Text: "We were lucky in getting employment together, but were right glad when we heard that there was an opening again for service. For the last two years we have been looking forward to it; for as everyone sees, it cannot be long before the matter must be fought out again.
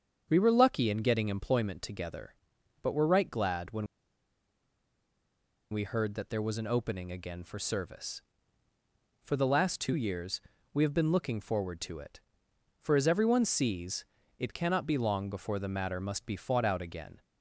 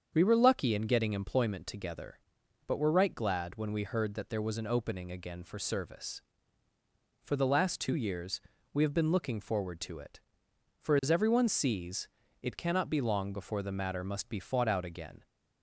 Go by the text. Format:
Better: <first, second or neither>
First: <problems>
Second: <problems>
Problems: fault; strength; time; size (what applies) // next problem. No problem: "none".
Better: second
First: starts louder than the rest; strong; until 1.3 s; 7 dB // pauses between "when" and "we"; strong; at 3.8 s; 1.8 s long // pauses between "years" and "we"; slight; at 10.4 s; 0.34 s long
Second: starts louder than the rest; strong; until 1.1 s; 7 dB // pauses between "years" and "we"; slight; at 8.4 s; 0.34 s long